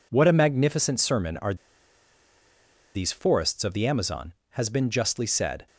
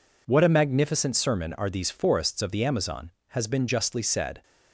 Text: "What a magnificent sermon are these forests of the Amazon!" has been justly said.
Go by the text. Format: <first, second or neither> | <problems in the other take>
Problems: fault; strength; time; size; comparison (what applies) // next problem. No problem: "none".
second | pauses between "are" and "these"; strong; at 1.5 s; 1.4 s long